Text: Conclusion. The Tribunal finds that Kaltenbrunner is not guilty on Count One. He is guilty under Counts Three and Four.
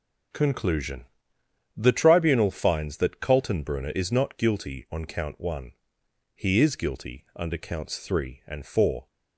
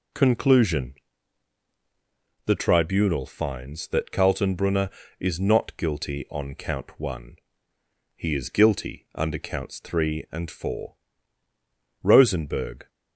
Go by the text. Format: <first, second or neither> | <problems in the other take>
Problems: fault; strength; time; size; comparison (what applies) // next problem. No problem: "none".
first | goes on to say "ROSENBERG"; noticeable; from 12.0 s on; 0.86 s long